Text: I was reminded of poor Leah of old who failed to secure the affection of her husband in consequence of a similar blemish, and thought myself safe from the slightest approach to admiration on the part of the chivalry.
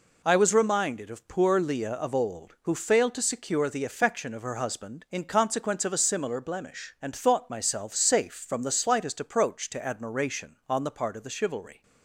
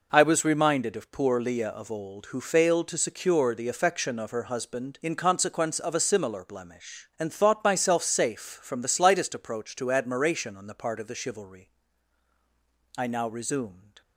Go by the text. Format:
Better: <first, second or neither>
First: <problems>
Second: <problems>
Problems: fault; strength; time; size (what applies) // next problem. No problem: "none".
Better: first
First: none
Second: goes on to say "I now resumed"; noticeable; from 12.9 s on; 1.0 s long